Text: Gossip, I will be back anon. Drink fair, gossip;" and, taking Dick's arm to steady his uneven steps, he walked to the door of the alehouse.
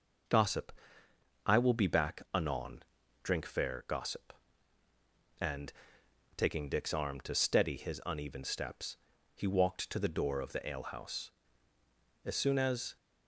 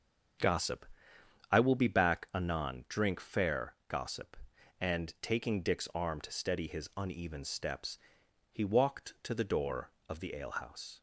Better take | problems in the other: second | starts louder than the rest; noticeable; until 2.0 s; 6 dB; also in the second // goes on to say "As soon as"; noticeable; from 12.2 s on; 0.72 s long

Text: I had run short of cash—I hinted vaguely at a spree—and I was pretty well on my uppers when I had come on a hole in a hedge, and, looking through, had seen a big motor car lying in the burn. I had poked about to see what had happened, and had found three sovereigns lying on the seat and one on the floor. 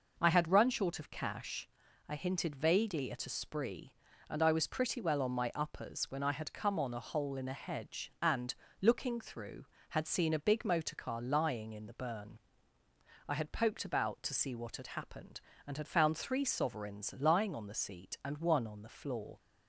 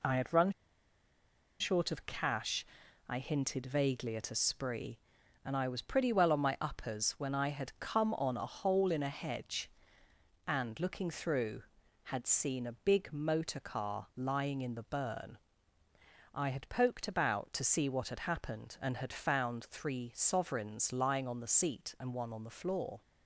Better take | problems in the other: first | pauses between "run" and "short"; at 0.5 s; 1.0 s long

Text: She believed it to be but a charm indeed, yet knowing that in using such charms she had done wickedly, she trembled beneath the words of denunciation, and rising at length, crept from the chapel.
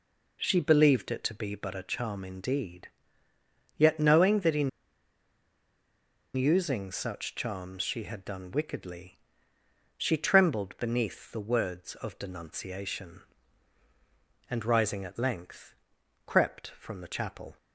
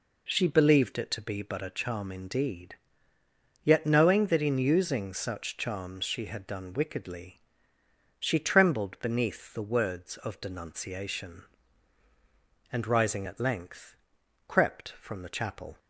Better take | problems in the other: second | pauses between "in" and "using"; strong; at 4.6 s; 1.6 s long

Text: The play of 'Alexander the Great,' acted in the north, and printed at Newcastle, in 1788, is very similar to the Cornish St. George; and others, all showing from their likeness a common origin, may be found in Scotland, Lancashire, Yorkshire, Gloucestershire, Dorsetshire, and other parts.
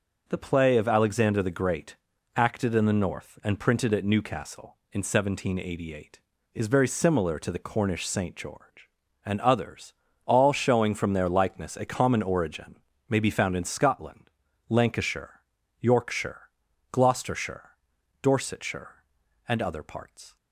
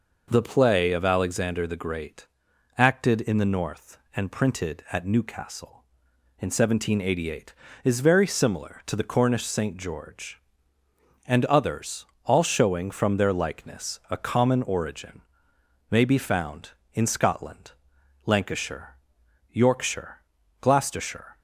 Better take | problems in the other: first | stops before "Dorsetshire and other parts"; at 21.3 s

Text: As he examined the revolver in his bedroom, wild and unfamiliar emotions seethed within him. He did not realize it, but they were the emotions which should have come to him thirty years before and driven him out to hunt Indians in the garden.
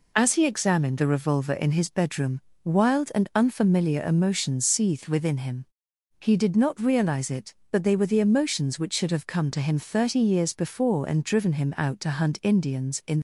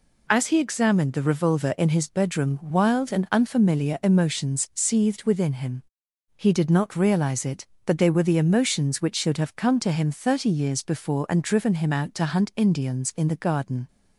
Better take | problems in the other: second | stops before "the garden"; at 13.1 s

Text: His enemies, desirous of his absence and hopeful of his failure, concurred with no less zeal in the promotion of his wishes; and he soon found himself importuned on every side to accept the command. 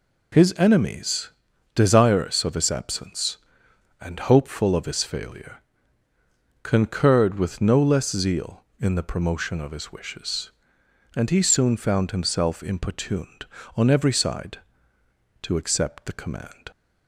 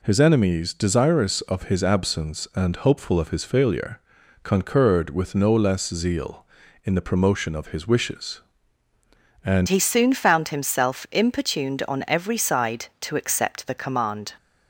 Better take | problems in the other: first | changes voice at "he"; from 9.6 s on; 4.7 s long

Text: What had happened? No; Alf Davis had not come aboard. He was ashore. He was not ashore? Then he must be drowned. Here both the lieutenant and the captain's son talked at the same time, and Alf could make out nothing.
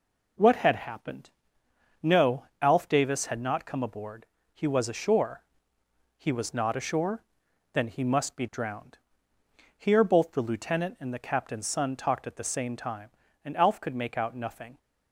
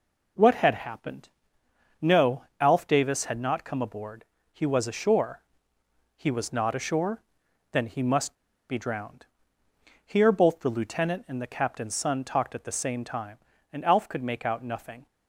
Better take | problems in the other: first | pauses between "must" and "be"; slight; at 8.3 s; 0.33 s long

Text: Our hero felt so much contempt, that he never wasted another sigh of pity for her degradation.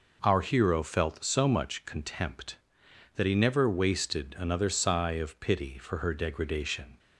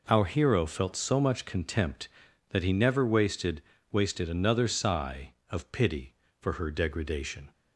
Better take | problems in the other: first | says "wasted" twice; at 3.9 s

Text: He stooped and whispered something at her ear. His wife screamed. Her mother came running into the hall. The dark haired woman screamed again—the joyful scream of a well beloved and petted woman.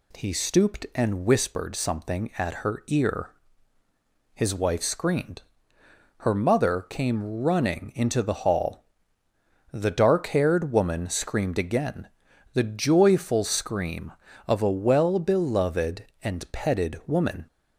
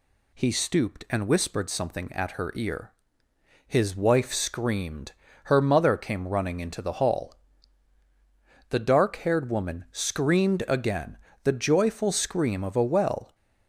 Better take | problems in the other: first | stops before "beloved and petted woman"; at 13.3 s

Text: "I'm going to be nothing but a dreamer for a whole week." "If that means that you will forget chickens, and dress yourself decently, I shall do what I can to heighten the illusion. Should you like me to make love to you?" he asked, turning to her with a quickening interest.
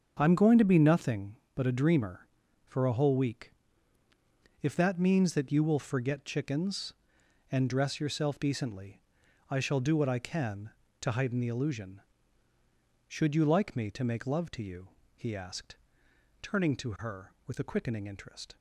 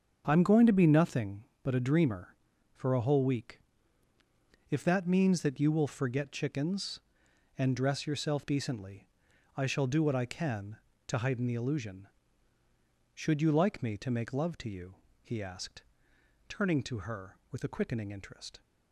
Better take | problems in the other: neither | starts louder than the rest; the same in both

